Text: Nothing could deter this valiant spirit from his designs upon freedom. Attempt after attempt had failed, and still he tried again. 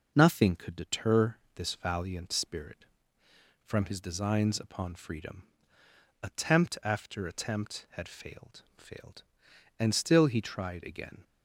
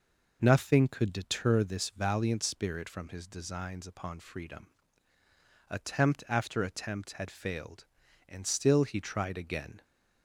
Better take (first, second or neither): second